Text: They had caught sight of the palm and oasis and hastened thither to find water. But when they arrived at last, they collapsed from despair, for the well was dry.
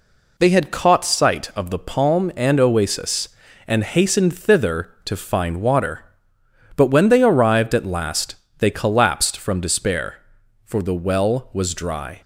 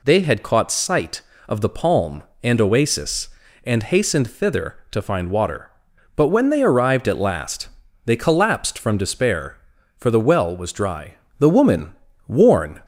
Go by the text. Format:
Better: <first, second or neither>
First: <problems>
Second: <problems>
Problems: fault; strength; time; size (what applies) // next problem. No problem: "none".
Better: first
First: none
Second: goes on to say "The woman worn"; from 11.3 s on; 1.4 s long